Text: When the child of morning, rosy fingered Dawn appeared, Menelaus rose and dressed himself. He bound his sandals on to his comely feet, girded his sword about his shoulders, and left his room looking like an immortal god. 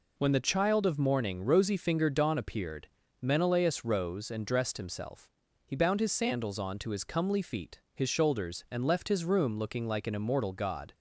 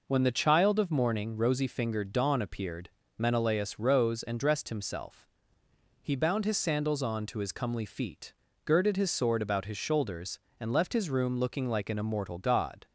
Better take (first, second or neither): second